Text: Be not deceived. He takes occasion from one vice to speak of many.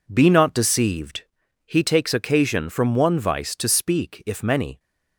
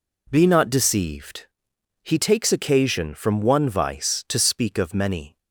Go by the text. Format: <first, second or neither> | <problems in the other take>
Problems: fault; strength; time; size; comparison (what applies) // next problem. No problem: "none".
second | says "if" for "of"; at 4.2 s